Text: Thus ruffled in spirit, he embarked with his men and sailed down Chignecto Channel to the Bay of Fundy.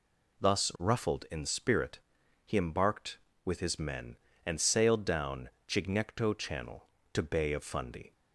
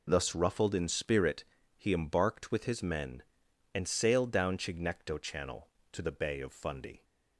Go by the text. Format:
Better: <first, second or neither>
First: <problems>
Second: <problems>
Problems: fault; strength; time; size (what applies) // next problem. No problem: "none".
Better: second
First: pauses between "down" and "Chignecto"; slight; at 5.4 s; 0.18 s long // skips "the"; at 7.2 s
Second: none